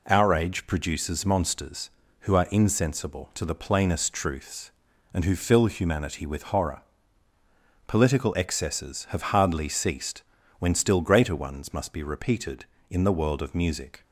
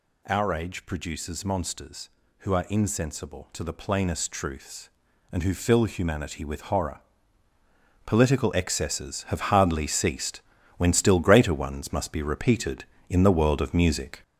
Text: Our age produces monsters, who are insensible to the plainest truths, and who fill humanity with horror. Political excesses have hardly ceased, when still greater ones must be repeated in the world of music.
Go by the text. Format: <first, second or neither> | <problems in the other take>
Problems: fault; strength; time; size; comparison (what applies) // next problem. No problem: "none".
first | gets louder; noticeable; throughout; 6 dB